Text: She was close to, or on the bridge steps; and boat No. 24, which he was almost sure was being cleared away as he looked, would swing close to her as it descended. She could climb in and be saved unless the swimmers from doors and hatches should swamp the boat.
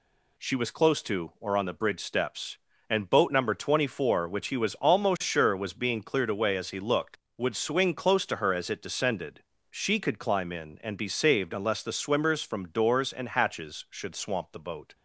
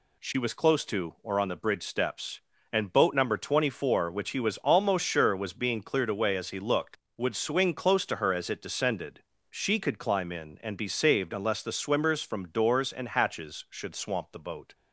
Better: neither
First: none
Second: none

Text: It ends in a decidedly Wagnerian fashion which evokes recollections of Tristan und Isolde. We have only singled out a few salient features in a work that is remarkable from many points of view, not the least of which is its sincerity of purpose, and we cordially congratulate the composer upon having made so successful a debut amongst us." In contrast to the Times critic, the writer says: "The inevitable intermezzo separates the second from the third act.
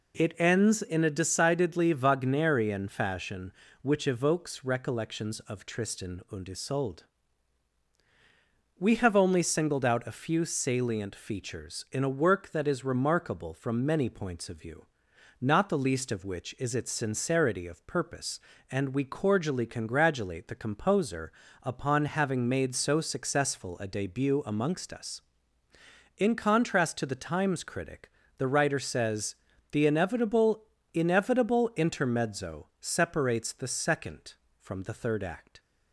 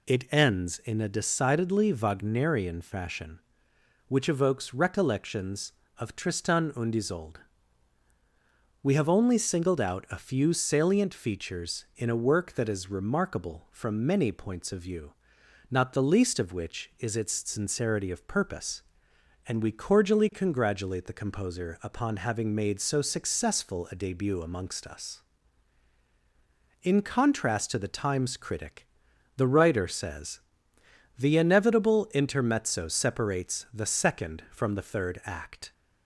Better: second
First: pauses between "composer" and "upon"; slight; at 21.2 s; 0.32 s long // says "inevitable" twice; at 30.9 s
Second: none

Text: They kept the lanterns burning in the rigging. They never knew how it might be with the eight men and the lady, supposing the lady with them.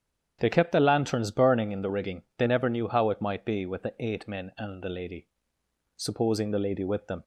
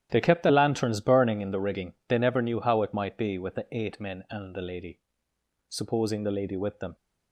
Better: first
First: starts louder than the rest; strong; until 1.4 s; 9 dB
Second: gets quieter; strong; throughout; 12.5 dB // starts louder than the rest; strong; until 1.1 s; 11 dB

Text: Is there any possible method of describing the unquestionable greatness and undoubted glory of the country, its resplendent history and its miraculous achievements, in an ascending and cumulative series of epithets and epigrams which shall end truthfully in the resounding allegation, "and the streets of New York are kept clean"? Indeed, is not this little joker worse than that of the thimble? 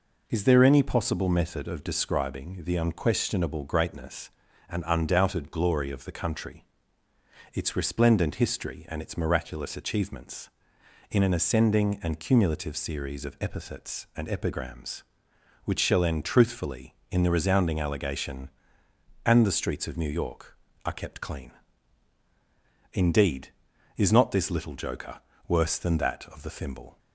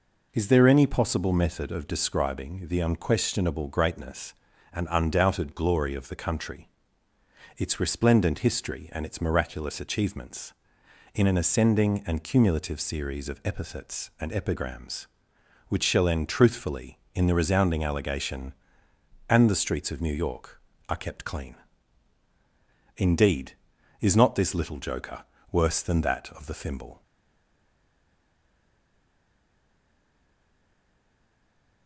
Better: first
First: pauses between "joker" and "worse"; slight; at 25.1 s; 0.28 s long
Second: pauses between "joker" and "worse"; slight; at 25.2 s; 0.28 s long // stays silent after the last word; strong; from 27.0 s on; 4.8 s long

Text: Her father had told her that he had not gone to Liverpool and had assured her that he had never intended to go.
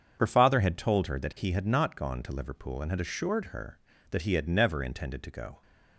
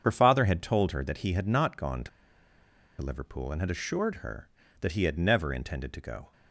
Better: first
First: starts louder than the rest; until 1.2 s; 7 dB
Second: starts louder than the rest; until 1.0 s; 7 dB // pauses between "to" and "Liverpool"; noticeable; at 2.0 s; 0.92 s long

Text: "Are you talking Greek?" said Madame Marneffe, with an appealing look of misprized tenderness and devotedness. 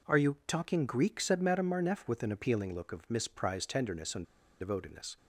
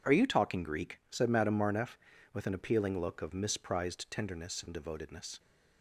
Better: second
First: pauses between "and" and "devotedness"; slight; at 4.2 s; 0.35 s long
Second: none

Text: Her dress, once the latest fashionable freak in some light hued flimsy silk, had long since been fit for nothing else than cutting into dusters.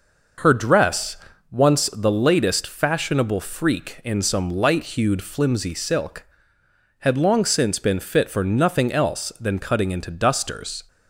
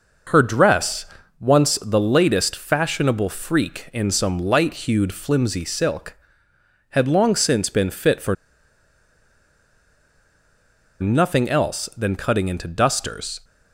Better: first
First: none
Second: pauses between "for" and "nothing"; strong; at 8.3 s; 2.6 s long

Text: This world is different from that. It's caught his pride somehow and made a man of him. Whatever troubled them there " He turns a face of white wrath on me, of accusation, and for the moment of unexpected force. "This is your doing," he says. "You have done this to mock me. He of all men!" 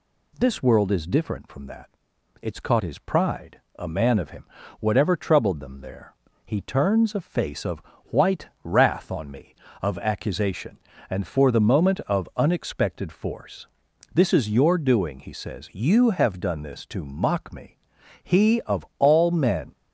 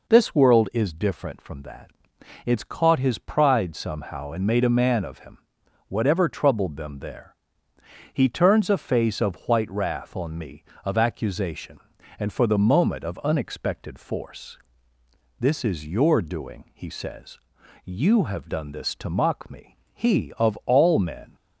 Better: second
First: skips "somehow and made"; at 3.6 s // pauses between "of" and "white"; slight; at 7.8 s; 0.22 s long // pauses between "white" and "wrath"; slight; at 8.4 s; 0.16 s long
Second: none

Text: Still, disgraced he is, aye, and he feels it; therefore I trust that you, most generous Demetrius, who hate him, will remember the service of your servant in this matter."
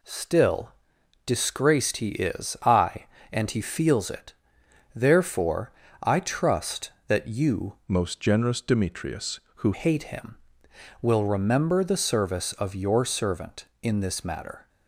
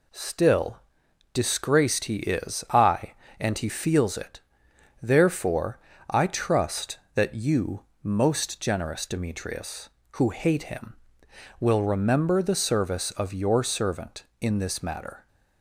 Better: second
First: pauses between "therefore" and "I"; slight; at 5.7 s; 0.30 s long // changes voice from "most" to "who"; from 7.8 to 9.7 s; 1.9 s long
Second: pauses between "therefore" and "I"; slight; at 5.7 s; 0.30 s long

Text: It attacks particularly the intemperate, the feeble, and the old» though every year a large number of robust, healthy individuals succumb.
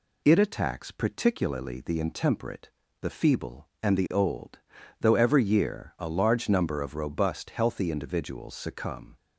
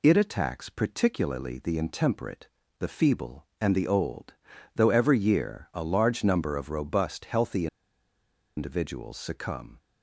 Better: first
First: pauses between "old" and "though"; at 4.5 s; 0.42 s long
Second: pauses between "old" and "though"; at 4.3 s; 0.42 s long // pauses between "healthy" and "individuals"; noticeable; at 7.6 s; 0.90 s long

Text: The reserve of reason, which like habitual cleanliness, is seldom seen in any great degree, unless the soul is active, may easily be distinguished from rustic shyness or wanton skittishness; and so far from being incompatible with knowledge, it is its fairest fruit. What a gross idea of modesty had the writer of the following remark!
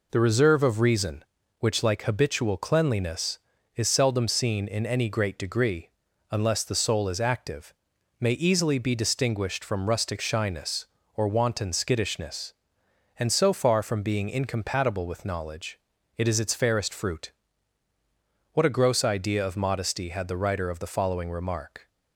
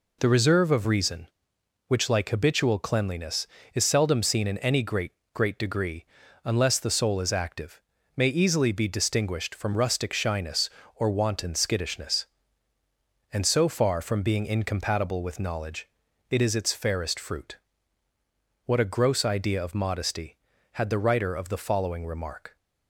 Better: first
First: none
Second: says "great" twice; at 5.3 s

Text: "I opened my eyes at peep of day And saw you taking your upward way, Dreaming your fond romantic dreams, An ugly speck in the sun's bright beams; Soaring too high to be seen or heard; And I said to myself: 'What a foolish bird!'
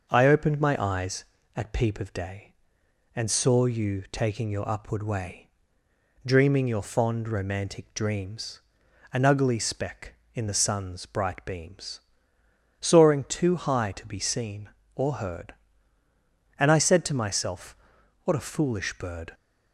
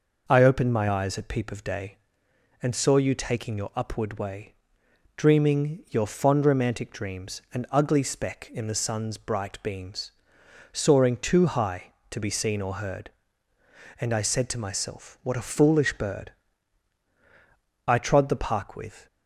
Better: first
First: none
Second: goes on to say "I trod the park with"; noticeable; from 17.8 s on; 1.2 s long

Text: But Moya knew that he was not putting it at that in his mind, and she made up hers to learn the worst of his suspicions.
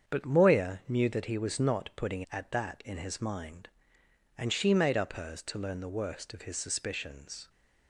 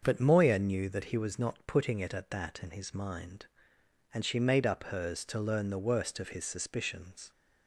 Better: second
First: starts louder than the rest; strong; until 1.1 s; 7 dB // skips "it"; at 2.2 s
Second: starts louder than the rest; until 1.0 s; 6.5 dB

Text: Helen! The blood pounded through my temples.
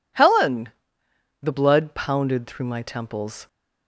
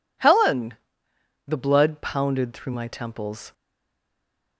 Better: first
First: none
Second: stays silent after the last word; from 3.5 s on; 1.0 s long

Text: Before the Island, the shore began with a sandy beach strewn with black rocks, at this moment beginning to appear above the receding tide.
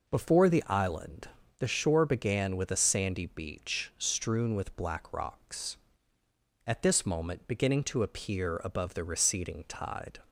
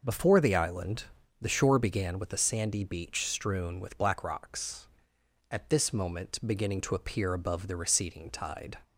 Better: neither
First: none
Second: none

